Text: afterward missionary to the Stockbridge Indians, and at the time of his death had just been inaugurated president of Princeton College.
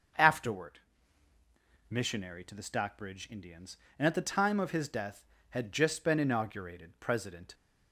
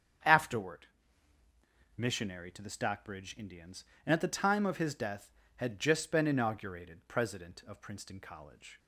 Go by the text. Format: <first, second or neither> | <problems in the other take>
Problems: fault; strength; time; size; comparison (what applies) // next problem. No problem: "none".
second | starts louder than the rest; until 2.2 s; 6.5 dB; strong in the second // pauses between "afterward" and "missionary"; at 0.7 s; 1.1 s long; also in the second // stops before "of Princeton College"; at 7.5 s